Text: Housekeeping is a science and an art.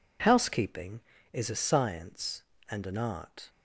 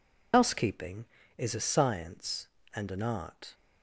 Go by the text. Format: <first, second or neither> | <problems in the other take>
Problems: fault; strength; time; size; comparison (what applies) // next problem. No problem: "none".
first | loses the start of "Housekeeping"; at 0.3 s; 90 ms